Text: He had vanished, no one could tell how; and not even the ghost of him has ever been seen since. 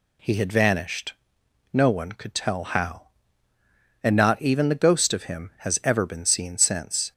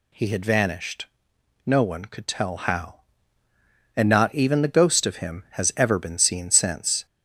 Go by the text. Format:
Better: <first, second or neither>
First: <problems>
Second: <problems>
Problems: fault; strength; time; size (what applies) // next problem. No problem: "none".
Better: first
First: none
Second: gets louder; slight; throughout; 3 dB